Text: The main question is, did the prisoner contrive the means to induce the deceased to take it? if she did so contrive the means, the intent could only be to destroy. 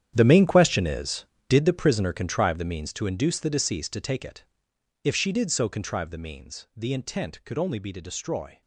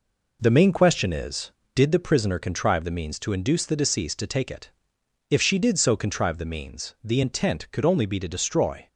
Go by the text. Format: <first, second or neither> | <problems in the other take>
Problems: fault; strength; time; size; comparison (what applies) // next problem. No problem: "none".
second | gets quieter; strong; throughout; 15.5 dB